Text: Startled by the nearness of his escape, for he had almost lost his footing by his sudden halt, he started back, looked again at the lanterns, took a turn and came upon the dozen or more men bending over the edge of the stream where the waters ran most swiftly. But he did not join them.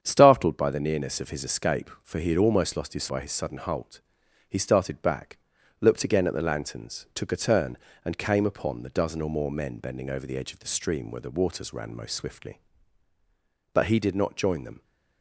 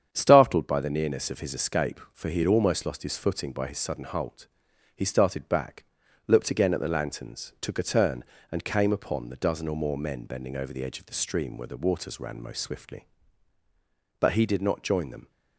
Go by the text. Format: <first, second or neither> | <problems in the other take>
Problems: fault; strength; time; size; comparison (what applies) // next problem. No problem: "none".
second | starts louder than the rest; strong; until 1.0 s; 8 dB; strong in the second // skips "footing"; at 3.0 s